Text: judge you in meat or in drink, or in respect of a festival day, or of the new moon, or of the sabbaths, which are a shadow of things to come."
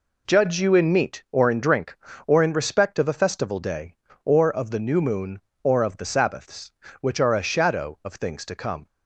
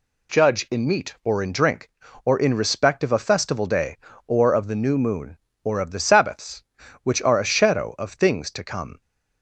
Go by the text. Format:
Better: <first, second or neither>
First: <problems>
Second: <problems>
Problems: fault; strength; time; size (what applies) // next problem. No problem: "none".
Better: first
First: none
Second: skips "you"; at 0.6 s